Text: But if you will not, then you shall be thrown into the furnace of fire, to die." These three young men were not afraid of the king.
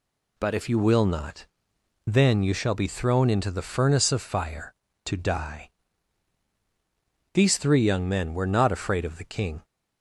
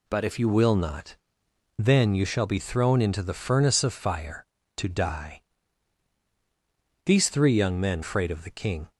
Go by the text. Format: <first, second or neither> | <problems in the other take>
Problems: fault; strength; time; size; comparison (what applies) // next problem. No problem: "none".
first | skips "were not"; at 8.0 s